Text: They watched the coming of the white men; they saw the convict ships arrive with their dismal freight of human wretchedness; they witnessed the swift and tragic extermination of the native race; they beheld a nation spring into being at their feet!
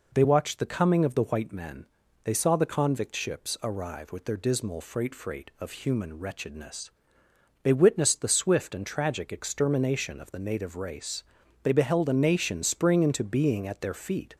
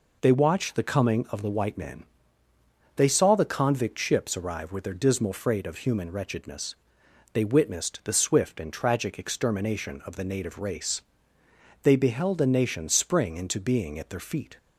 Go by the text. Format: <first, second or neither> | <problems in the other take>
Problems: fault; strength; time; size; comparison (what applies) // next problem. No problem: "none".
second | says "freight" twice; at 5.1 s